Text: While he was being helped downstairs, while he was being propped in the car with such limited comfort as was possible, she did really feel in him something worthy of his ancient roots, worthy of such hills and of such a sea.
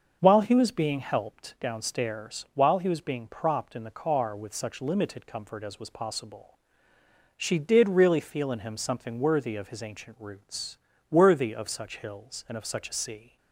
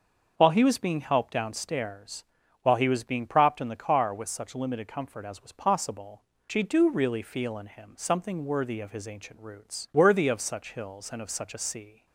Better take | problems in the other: first | starts louder than the rest; until 1.3 s; 6.5 dB; also in the first // says "do" for "did"; at 6.6 s

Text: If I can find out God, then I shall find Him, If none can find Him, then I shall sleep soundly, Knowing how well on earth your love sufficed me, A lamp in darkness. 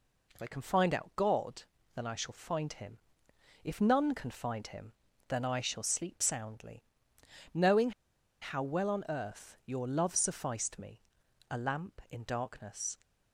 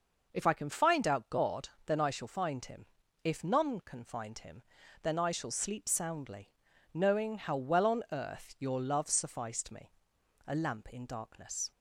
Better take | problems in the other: second | pauses between "Knowing" and "how"; noticeable; at 7.9 s; 0.50 s long

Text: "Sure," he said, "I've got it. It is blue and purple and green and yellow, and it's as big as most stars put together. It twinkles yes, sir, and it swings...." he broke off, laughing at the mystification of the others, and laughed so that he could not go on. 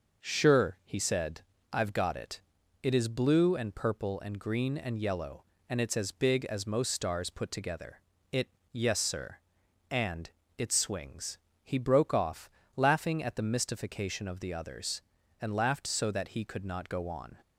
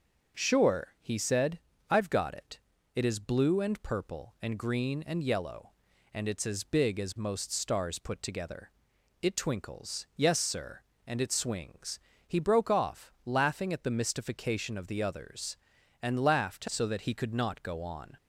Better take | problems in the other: second | starts louder than the rest; noticeable; until 1.3 s; 6 dB; also in the second // skips "twinkles"; at 8.6 s // pauses between "and" and "it"; slight; at 10.2 s; 0.28 s long

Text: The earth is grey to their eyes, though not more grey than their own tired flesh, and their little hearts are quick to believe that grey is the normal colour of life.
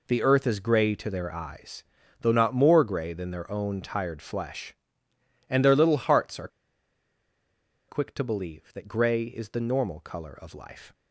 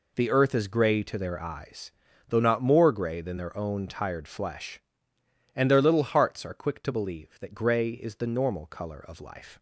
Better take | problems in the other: second | pauses between "are" and "quick"; strong; at 6.4 s; 1.4 s long

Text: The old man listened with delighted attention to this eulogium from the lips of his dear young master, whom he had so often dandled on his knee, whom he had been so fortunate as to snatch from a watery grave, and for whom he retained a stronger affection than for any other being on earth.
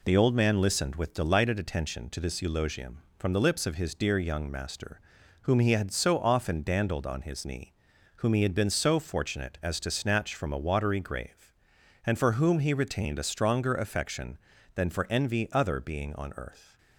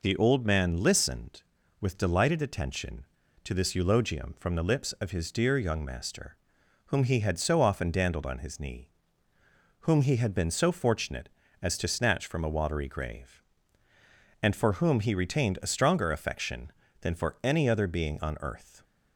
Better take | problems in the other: second | says "envy" for "any"; at 15.0 s

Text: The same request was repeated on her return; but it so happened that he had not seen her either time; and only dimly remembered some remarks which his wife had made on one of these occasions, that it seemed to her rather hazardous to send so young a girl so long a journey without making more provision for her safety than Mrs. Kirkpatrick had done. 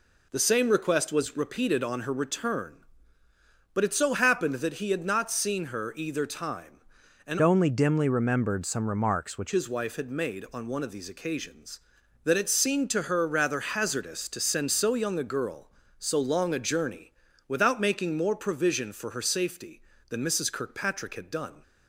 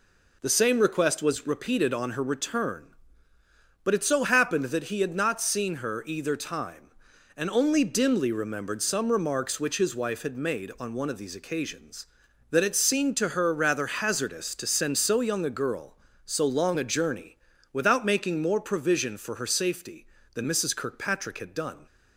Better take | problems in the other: second | changes voice from "only" to "which"; from 7.4 to 9.5 s; 2.1 s long // pauses between "journey" and "without"; slight; at 17.1 s; 0.34 s long; slight in the second

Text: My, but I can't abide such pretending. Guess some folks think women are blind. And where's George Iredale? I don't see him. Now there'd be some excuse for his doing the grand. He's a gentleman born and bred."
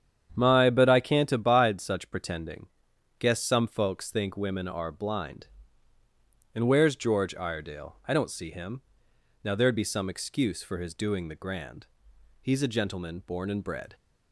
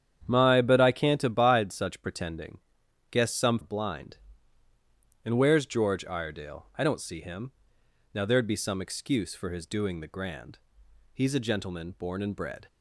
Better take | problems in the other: first | starts louder than the rest; strong; until 1.2 s; 9 dB; strong in the first // skips "folks think women are"; at 3.5 s

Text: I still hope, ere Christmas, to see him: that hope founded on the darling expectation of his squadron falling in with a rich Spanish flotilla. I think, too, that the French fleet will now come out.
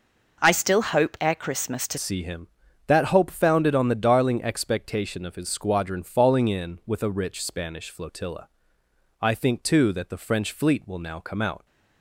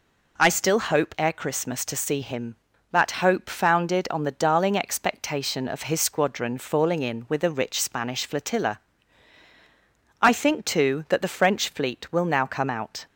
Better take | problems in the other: second | changes voice at "see"; from 1.9 s on; 9.7 s long

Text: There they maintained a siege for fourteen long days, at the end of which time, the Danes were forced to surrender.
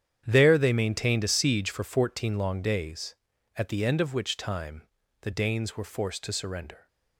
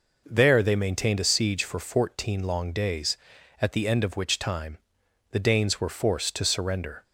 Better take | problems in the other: second | gets quieter; strong; throughout; 14 dB

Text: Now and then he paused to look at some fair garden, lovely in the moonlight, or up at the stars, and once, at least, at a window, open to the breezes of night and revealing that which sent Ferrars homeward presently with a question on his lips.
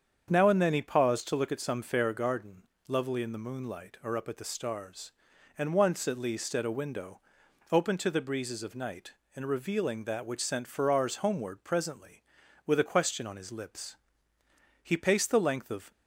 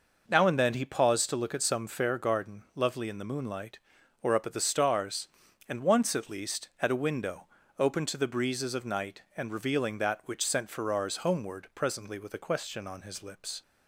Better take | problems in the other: second | starts louder than the rest; strong; until 1.3 s; 7.5 dB // goes on to say "He paced the length of"; noticeable; from 14.8 s on; 1.0 s long

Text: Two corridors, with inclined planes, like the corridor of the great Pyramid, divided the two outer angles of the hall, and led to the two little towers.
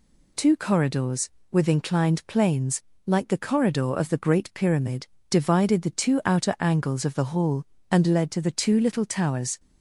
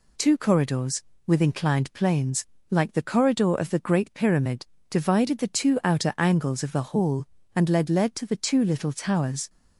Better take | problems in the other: first | says "led" twice; at 7.8 s

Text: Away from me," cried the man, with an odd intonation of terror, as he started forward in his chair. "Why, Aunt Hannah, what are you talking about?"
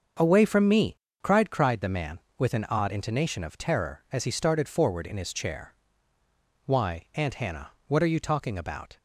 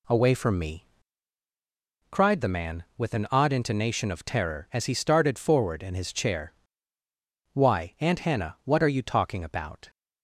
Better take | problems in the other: second | starts louder than the rest; until 1.4 s; 6.5 dB // says "cried" twice; at 1.5 s

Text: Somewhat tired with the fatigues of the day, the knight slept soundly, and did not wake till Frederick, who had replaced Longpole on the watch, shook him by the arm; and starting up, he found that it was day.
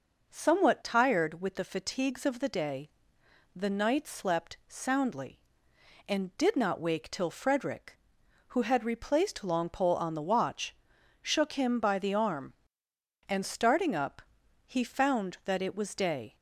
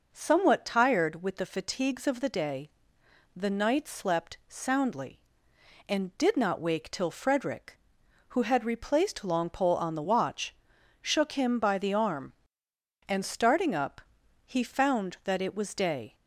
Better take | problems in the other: neither | none

